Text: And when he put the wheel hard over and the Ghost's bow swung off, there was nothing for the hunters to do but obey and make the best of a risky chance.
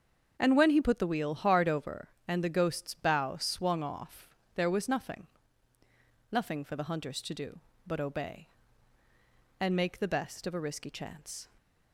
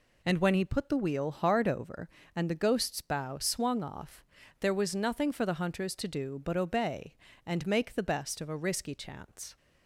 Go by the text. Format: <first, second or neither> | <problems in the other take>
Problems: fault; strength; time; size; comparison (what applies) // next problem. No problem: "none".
second | starts louder than the rest; until 1.4 s; 7 dB // says "nothing" twice; at 6.2 s